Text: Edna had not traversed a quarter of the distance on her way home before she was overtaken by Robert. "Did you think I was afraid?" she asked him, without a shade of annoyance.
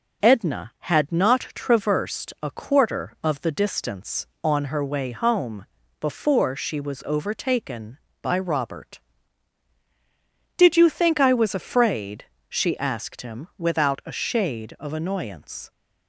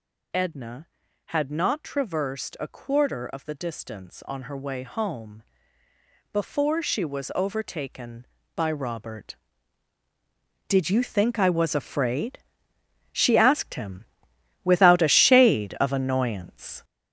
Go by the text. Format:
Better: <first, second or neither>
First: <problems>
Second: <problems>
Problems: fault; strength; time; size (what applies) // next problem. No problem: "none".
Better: first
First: pauses between "home" and "before"; slight; at 5.6 s; 0.34 s long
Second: gets louder; strong; throughout; 7 dB // pauses between "home" and "before"; noticeable; at 5.4 s; 0.90 s long